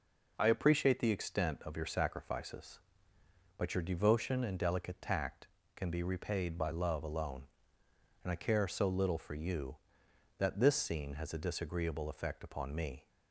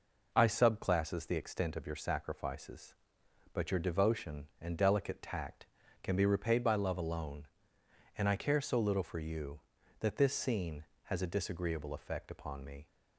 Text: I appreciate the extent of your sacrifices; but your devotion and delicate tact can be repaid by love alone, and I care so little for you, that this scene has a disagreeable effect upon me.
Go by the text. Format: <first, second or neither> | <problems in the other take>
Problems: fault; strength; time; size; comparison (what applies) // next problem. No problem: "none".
first | says "subclasses" for "appreciate"; at 0.4 s